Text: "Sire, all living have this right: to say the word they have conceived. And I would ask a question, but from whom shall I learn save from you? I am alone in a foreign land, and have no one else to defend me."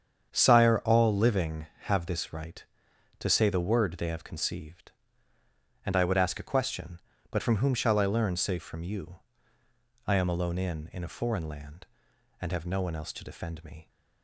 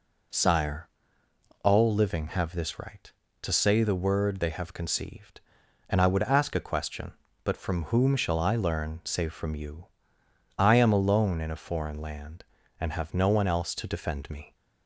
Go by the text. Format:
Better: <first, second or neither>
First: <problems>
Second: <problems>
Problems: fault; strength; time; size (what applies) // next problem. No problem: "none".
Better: second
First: starts louder than the rest; strong; until 1.3 s; 8 dB // says "in" twice; at 10.9 s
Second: none